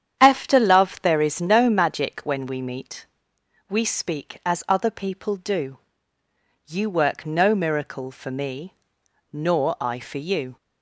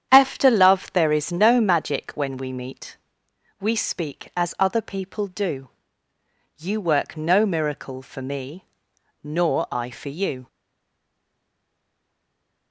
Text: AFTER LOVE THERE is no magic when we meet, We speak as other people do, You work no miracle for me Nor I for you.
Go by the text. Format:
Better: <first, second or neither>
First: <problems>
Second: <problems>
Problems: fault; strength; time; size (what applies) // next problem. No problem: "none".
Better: first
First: starts louder than the rest; strong; until 1.2 s; 9 dB // pauses between "me" and "Nor"; noticeable; at 8.7 s; 0.58 s long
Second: starts louder than the rest; strong; until 1.1 s; 9 dB // pauses between "me" and "Nor"; noticeable; at 8.6 s; 0.58 s long // stays silent after the last word; from 10.4 s on; 2.3 s long